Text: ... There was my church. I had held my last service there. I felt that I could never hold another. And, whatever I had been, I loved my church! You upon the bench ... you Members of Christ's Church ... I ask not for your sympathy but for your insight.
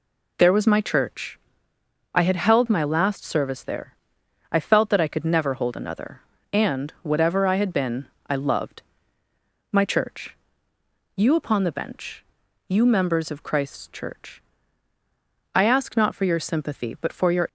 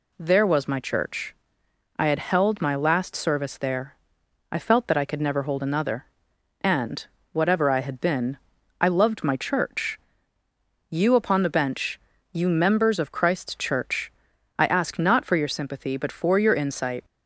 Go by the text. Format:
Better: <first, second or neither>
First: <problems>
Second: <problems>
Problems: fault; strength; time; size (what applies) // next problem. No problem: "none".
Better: second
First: pauses between "loved" and "my"; noticeable; at 8.8 s; 0.90 s long // stops before "insight"; at 17.4 s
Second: none